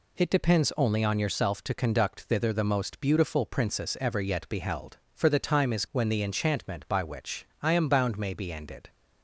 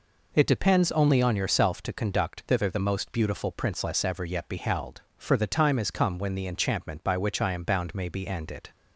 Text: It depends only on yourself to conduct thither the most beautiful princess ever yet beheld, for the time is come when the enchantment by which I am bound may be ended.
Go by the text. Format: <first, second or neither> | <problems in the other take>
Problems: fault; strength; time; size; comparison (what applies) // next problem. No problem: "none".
second | skips "come"; at 5.8 s // pauses between "which" and "I"; slight; at 7.4 s; 0.16 s long